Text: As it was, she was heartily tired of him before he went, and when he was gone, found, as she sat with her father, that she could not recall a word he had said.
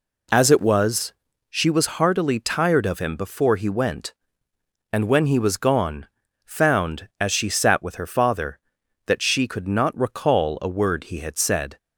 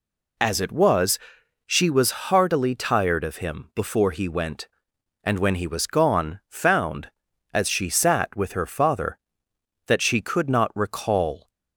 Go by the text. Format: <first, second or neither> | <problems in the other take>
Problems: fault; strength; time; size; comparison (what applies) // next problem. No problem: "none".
first | stops before "a word he had said"; at 11.4 s